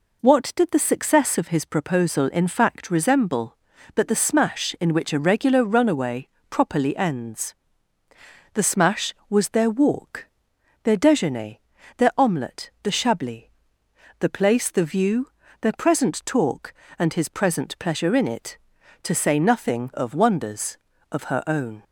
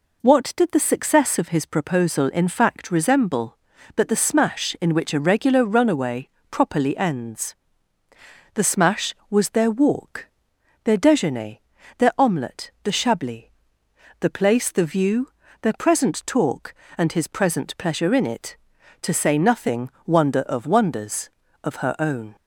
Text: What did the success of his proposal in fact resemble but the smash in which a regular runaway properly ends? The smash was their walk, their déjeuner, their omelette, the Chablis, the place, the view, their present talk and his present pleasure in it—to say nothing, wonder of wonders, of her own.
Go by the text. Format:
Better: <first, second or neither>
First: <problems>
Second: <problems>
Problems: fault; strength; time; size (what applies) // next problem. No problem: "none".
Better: second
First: pauses between "runaway" and "properly"; slight; at 6.2 s; 0.22 s long // skips "wonder"; at 19.9 s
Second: pauses between "runaway" and "properly"; slight; at 6.2 s; 0.22 s long